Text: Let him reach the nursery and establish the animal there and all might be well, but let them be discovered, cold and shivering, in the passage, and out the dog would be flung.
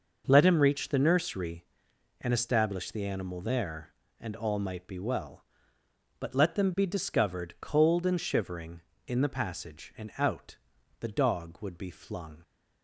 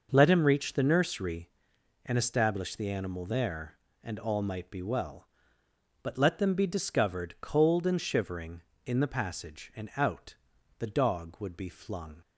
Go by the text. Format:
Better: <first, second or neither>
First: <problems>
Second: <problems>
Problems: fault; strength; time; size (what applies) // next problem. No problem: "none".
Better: neither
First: pauses between "out" and "the"; at 10.5 s; 0.44 s long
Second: pauses between "out" and "the"; at 10.3 s; 0.44 s long